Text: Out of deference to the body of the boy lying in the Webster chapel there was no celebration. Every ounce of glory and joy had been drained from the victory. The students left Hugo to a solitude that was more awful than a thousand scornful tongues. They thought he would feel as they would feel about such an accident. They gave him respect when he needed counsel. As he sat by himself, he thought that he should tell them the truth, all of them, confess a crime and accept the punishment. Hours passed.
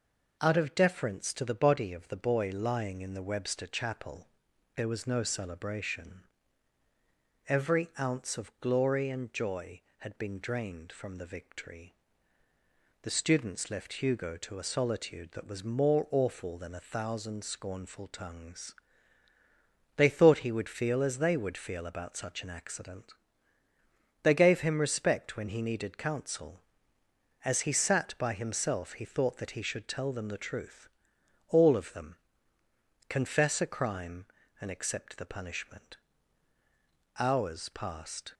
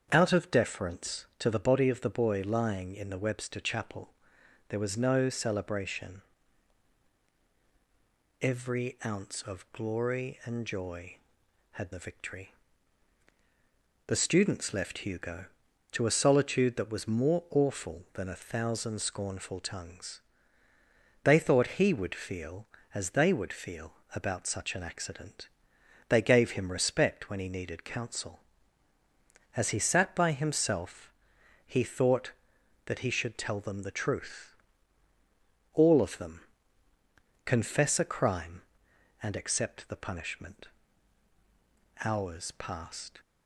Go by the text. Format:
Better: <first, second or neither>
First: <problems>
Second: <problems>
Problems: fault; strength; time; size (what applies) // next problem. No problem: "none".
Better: first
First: pauses between "chapel" and "there"; noticeable; at 4.2 s; 0.50 s long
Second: starts louder than the rest; strong; until 1.1 s; 7.5 dB // pauses between "chapel" and "there"; noticeable; at 4.0 s; 0.60 s long // skips "been drained from"; at 11.9 s // pauses between "feel" and "about"; slight; at 23.9 s; 0.24 s long